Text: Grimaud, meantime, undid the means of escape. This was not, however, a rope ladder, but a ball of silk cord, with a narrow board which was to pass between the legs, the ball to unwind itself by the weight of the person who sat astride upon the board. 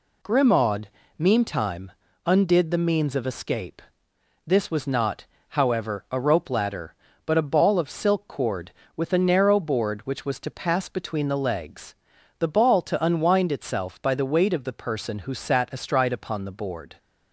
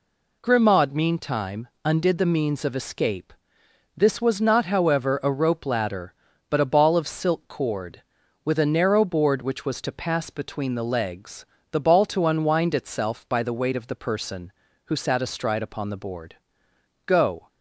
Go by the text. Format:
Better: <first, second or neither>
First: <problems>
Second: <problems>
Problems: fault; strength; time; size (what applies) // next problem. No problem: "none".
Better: first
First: none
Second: goes on to say "Go"; slight; from 17.0 s on; 0.44 s long